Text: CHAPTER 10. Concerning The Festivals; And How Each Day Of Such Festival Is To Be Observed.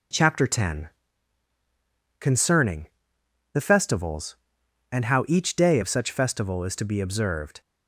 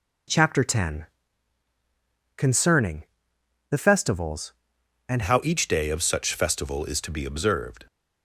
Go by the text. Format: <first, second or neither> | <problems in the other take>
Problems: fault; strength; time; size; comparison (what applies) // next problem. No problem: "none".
first | pauses between "Concerning" and "The"; noticeable; at 3.0 s; 0.66 s long; noticeable in the first // changes voice at "How"; from 5.2 s on; 2.6 s long